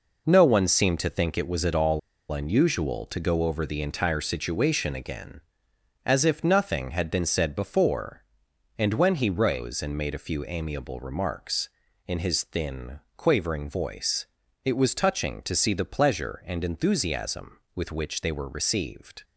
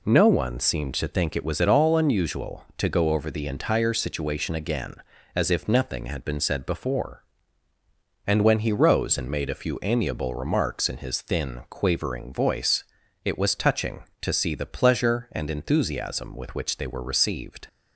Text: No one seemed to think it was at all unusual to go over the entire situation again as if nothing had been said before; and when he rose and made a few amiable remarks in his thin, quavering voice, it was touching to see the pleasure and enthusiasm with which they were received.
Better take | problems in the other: second | pauses between "all" and "unusual"; slight; at 1.9 s; 0.31 s long

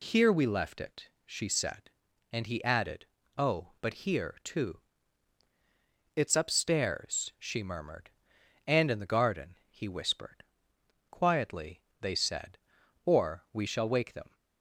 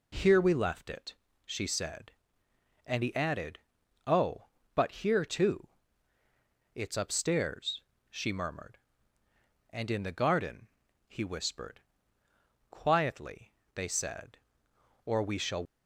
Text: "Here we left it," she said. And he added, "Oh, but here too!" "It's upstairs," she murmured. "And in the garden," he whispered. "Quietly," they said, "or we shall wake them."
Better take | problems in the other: first | stops before "wake them"; at 15.6 s

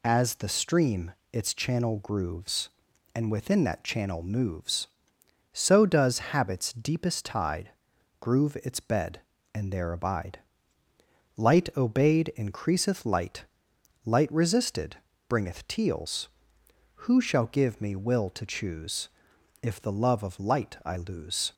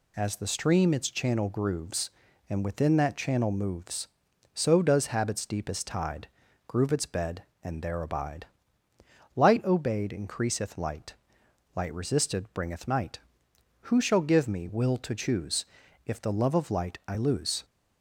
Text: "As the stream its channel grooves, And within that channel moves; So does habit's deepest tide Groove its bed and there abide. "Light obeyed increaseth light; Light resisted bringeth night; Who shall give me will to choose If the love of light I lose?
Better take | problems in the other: second | pauses between "stream" and "its"; slight; at 1.1 s; 0.20 s long // pauses between "tide" and "Groove"; noticeable; at 7.7 s; 0.48 s long; also in the second // pauses between "resisted" and "bringeth"; slight; at 14.9 s; 0.30 s long // says "teals" for "night"; at 15.6 s // pauses between "choose" and "If"; noticeable; at 19.0 s; 0.56 s long; also in the second

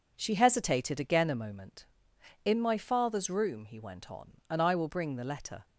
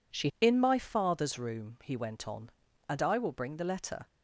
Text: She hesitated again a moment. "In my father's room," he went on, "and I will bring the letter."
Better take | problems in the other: first | skips "hesitated again a moment"; at 0.3 s

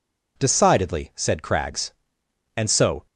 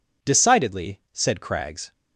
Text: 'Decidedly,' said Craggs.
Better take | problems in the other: second | goes on to say "And so"; slight; from 2.5 s on; 0.48 s long

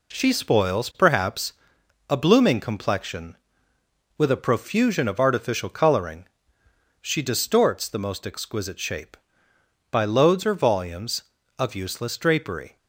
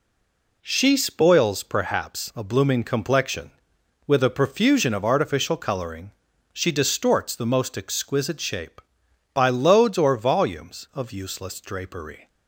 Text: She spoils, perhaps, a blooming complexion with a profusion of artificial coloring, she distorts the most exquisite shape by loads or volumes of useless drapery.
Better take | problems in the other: first | stays silent before the first word; slight; until 0.6 s; 0.6 s long

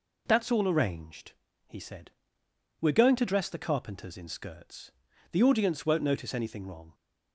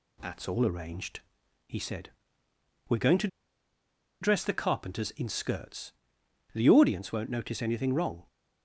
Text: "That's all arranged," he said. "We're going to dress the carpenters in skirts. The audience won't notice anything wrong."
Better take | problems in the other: first | pauses between "to" and "dress"; noticeable; at 3.2 s; 0.94 s long

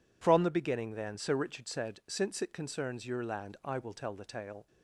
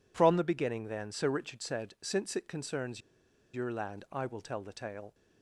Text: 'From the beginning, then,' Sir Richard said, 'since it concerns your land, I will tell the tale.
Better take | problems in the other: first | pauses between "concerns" and "your"; noticeable; at 3.0 s; 0.53 s long

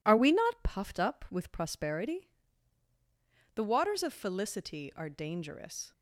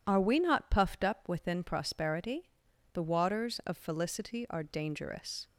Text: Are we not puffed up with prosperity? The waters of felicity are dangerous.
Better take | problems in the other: first | says "within" for "with"; at 1.2 s

